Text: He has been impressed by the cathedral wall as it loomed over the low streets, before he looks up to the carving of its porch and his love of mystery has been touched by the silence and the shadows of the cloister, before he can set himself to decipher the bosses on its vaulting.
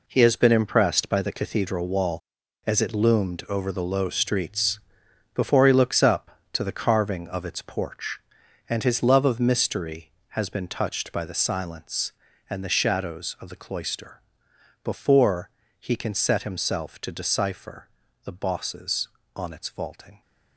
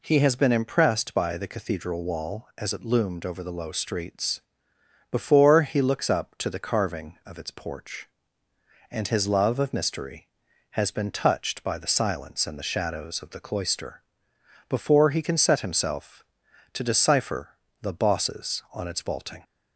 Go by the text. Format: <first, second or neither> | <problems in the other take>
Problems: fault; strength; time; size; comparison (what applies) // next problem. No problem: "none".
second | gets quieter; strong; throughout; 8.5 dB // pauses between "before" and "he"; slight; at 15.4 s; 0.30 s long // pauses between "decipher" and "the"; at 17.8 s; 0.38 s long; slight in the second